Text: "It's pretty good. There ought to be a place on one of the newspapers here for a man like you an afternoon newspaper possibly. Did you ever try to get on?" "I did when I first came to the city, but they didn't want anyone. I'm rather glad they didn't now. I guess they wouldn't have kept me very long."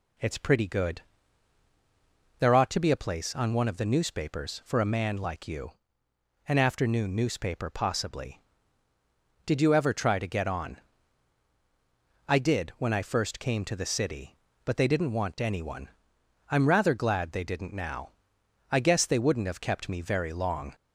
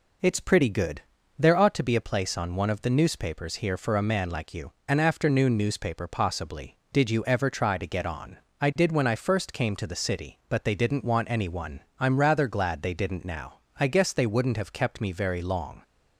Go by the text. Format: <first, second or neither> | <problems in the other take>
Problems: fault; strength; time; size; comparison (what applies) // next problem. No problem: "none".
second | skips "here"; at 4.6 s // pauses between "you" and "an"; noticeable; at 5.7 s; 0.78 s long